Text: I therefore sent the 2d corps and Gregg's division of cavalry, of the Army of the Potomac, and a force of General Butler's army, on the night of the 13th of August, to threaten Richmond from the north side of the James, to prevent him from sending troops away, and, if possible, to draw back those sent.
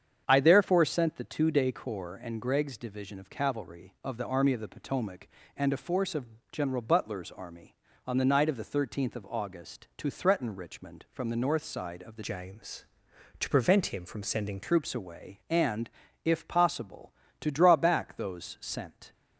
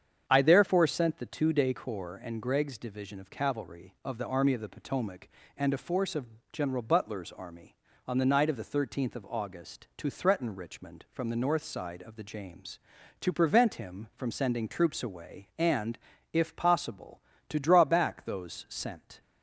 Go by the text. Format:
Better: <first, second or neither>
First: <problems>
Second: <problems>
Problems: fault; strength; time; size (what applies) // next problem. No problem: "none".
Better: second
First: starts louder than the rest; strong; until 1.2 s; 8 dB // pauses between "of" and "General"; slight; at 6.2 s; 0.24 s long // changes voice from "James" to "sending"; from 12.2 to 14.6 s; 2.4 s long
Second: starts louder than the rest; strong; until 1.2 s; 8 dB // pauses between "of" and "General"; slight; at 6.2 s; 0.24 s long